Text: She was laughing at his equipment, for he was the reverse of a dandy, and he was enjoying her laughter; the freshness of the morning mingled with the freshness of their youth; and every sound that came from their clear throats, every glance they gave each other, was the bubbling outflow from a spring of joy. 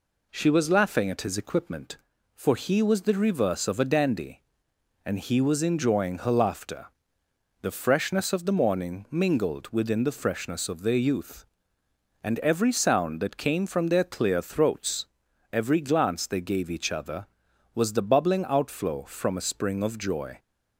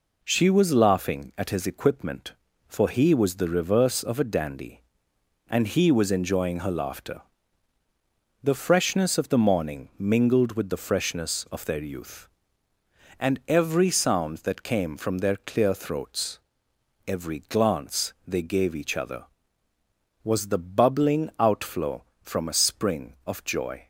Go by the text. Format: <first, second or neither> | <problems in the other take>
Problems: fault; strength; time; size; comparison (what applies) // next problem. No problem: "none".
second | says "within" for "with"; at 9.6 s